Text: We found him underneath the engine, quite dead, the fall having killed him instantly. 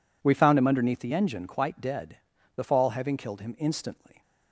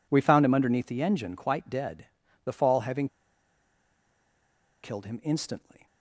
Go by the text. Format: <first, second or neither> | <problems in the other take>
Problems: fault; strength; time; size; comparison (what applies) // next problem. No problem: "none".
first | pauses between "having" and "killed"; strong; at 3.0 s; 1.7 s long